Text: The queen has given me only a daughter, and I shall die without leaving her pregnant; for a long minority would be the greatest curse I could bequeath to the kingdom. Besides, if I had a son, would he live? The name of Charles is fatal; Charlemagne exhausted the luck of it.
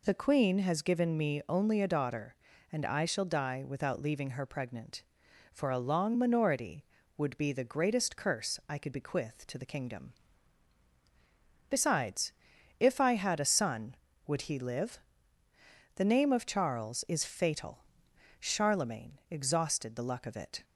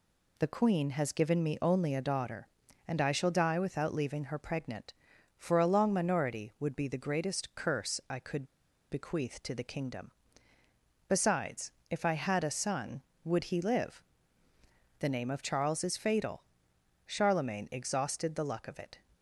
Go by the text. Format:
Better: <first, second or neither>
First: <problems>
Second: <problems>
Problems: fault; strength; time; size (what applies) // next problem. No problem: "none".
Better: first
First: none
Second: pauses between "could" and "bequeath"; noticeable; at 8.4 s; 0.46 s long